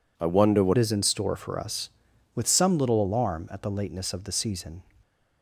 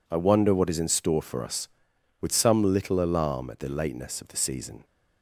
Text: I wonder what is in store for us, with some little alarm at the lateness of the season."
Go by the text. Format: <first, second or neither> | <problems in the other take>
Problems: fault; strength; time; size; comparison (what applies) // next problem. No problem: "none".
second | changes voice at "is"; from 0.7 s on; 4.1 s long